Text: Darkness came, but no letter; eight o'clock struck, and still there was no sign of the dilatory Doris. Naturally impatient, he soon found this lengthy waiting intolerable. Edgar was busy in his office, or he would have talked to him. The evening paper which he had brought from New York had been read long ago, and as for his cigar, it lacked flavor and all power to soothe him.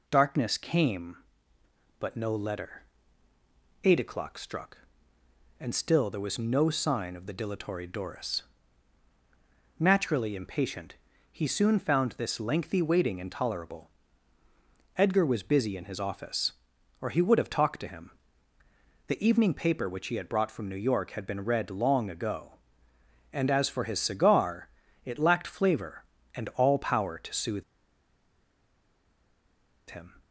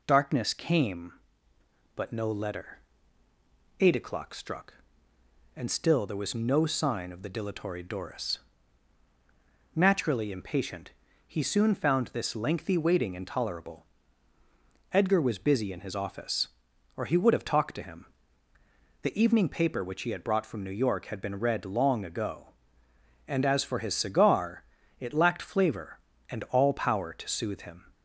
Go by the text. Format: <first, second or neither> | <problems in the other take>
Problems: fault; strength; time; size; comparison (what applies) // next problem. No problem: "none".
second | pauses between "soothe" and "him"; strong; at 27.6 s; 2.2 s long